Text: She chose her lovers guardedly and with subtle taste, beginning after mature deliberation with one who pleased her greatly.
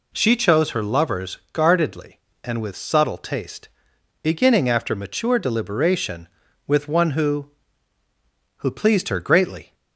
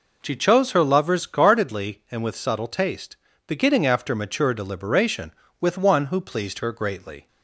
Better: second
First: says "who" twice; at 8.5 s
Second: none

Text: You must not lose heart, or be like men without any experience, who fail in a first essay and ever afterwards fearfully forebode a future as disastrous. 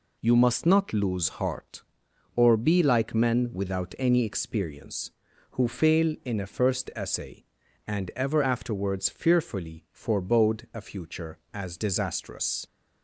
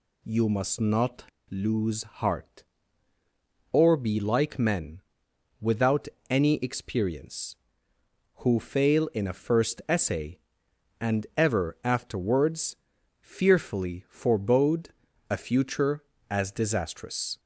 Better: first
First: none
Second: pauses between "not" and "lose"; slight; at 1.2 s; 0.25 s long // pauses between "men" and "without"; noticeable; at 5.0 s; 0.58 s long // pauses between "without" and "any"; slight; at 6.0 s; 0.22 s long // pauses between "afterwards" and "fearfully"; at 12.7 s; 0.44 s long // pauses between "forebode" and "a"; at 14.8 s; 0.40 s long

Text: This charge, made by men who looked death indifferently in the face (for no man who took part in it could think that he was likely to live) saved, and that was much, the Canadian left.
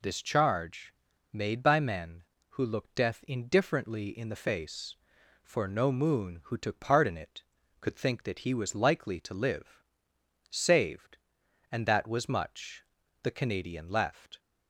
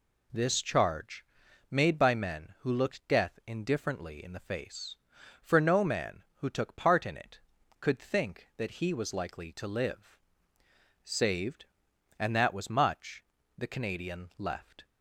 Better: second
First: says "moon" for "man"; at 5.9 s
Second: none

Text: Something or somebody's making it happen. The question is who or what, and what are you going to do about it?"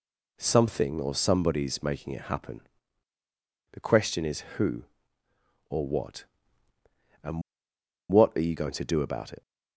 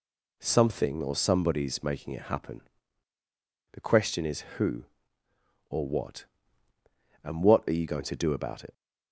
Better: second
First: pauses between "and" and "what"; noticeable; at 7.4 s; 0.69 s long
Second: none

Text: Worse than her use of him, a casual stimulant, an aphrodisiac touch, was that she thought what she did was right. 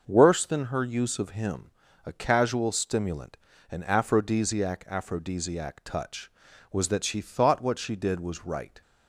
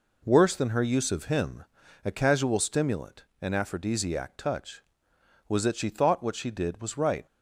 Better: second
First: says "aphrodisiac" twice; at 4.8 s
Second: none

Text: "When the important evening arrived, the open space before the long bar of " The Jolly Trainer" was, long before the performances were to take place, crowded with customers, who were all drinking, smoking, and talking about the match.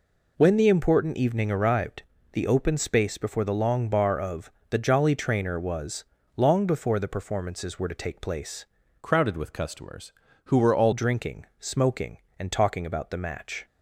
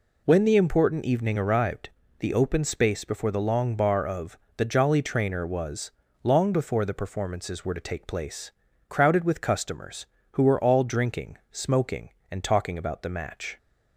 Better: second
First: changes voice from "crowded" to "all"; from 9.0 to 10.9 s; 1.9 s long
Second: none

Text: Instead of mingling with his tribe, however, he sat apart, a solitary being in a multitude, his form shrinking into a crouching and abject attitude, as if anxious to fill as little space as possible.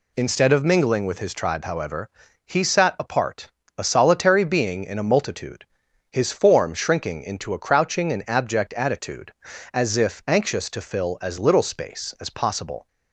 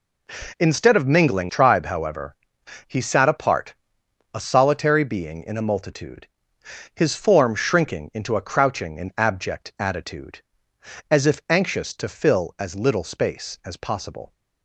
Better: first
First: none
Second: skips "with his"; at 1.4 s

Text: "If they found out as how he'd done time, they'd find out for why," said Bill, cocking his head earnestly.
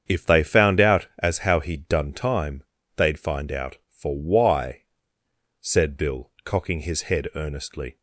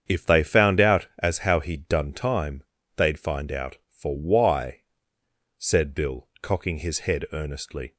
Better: neither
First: starts louder than the rest; strong; until 1.0 s; 7.5 dB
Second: starts louder than the rest; strong; until 1.0 s; 7.5 dB

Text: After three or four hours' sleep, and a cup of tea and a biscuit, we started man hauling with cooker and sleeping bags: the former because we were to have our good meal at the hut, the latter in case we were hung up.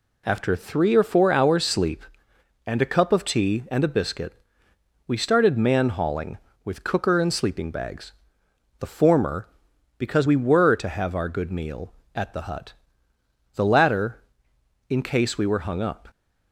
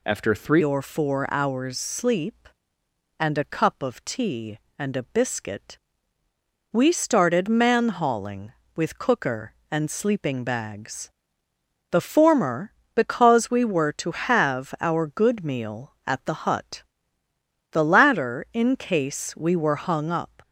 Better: first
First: none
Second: changes voice at "or"; from 0.6 s on; 19.8 s long

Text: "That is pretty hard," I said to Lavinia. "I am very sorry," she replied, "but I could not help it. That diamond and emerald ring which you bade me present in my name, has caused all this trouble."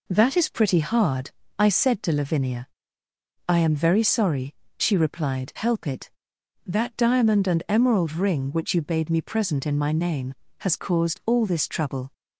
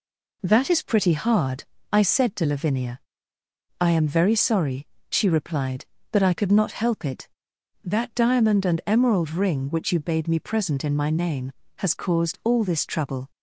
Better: second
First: skips "but I could not"; at 5.5 s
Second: none

